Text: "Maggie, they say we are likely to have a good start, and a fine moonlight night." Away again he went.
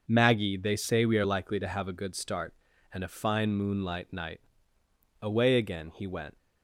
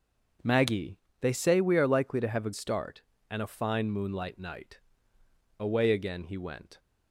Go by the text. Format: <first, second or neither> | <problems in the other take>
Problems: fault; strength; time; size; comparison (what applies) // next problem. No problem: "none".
first | starts louder than the rest; until 1.6 s; 6.5 dB // skips "good"; at 2.5 s